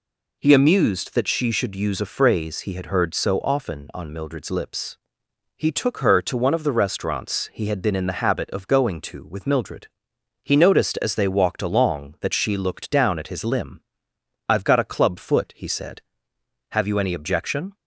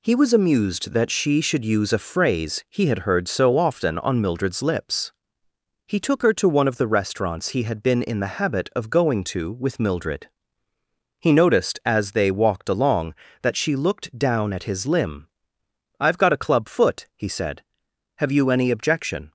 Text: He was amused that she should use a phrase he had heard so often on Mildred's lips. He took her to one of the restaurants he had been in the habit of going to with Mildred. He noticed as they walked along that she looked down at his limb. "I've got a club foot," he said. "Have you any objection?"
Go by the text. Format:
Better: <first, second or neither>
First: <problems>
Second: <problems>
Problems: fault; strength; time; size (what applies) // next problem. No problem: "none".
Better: second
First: skips "was"; at 0.5 s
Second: none